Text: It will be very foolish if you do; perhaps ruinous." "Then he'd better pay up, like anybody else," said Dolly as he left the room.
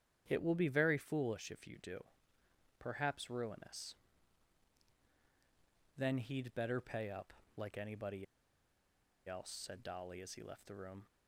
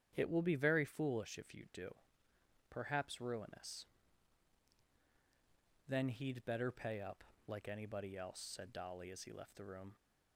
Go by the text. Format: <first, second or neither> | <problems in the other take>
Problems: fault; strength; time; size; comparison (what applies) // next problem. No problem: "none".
second | starts louder than the rest; strong; until 1.2 s; 9.5 dB; strong in the second // pauses between "anybody" and "else"; at 8.2 s; 1.0 s long